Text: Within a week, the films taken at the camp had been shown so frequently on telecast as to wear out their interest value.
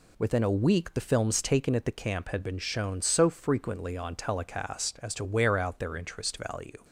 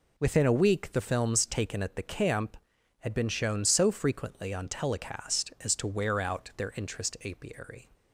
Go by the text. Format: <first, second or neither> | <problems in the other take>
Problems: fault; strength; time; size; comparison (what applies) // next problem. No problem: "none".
first | says "apiary" for "value"; at 7.2 s